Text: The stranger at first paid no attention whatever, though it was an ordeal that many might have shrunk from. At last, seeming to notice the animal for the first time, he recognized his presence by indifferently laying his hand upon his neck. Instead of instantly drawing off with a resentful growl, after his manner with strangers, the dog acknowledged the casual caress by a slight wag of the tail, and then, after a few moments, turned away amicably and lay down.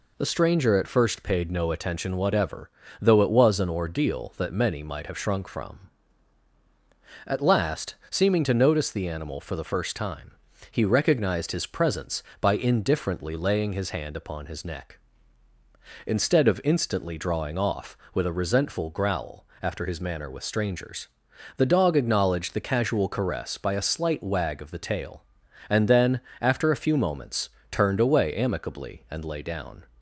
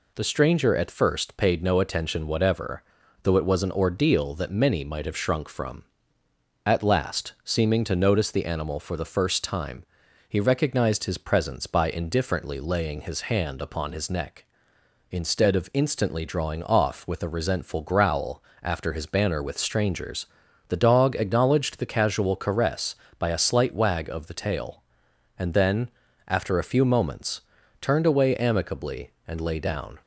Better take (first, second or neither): first